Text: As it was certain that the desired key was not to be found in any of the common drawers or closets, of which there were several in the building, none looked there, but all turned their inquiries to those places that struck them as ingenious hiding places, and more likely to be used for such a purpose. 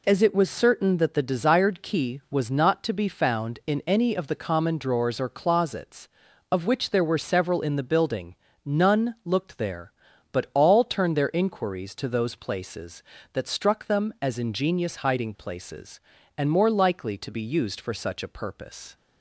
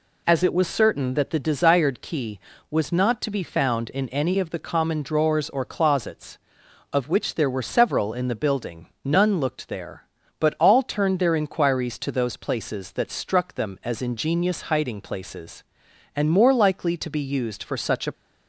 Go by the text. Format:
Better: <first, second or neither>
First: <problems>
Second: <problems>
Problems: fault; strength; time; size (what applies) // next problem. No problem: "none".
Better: first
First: none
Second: stops before "purpose"; at 18.1 s